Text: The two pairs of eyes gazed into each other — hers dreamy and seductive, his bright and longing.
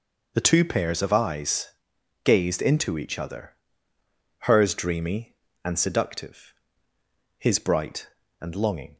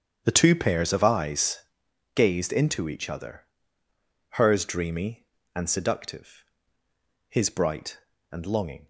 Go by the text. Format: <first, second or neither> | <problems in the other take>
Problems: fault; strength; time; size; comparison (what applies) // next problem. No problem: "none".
first | starts louder than the rest; strong; until 2.0 s; 8.5 dB // pauses between "eyes" and "gazed"; noticeable; at 1.5 s; 0.56 s long; noticeable in the first